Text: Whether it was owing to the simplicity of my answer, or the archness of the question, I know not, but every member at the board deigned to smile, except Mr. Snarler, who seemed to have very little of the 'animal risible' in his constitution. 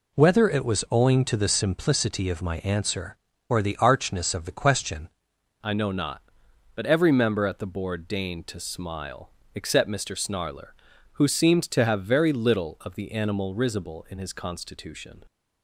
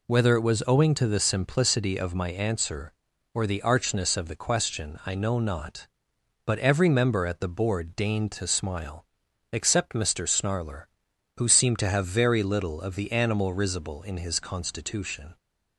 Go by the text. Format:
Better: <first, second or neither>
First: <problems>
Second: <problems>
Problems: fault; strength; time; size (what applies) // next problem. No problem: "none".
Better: second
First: changes voice at "I"; from 5.6 s on; 9.6 s long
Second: none